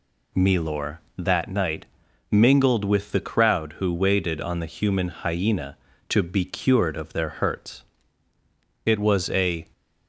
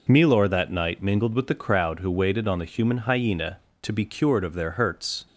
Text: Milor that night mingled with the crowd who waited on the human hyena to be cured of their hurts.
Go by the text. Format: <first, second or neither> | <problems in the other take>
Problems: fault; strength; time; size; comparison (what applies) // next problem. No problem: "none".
second | pauses between "night" and "mingled"; noticeable; at 1.8 s; 0.46 s long // goes on to say "It was a"; noticeable; from 8.8 s on; 0.84 s long